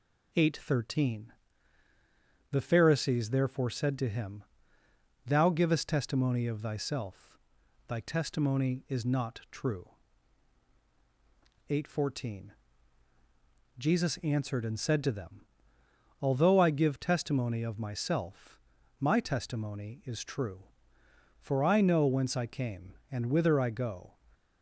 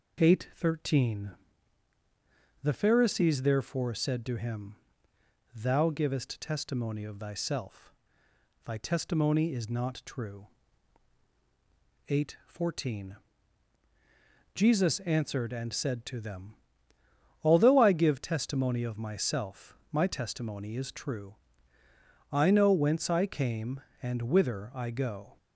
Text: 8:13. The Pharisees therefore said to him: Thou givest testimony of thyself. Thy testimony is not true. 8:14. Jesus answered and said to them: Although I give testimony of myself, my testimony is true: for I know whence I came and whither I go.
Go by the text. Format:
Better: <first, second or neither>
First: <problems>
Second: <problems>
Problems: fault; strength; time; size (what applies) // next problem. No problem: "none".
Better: first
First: none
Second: skips "for"; at 21.8 s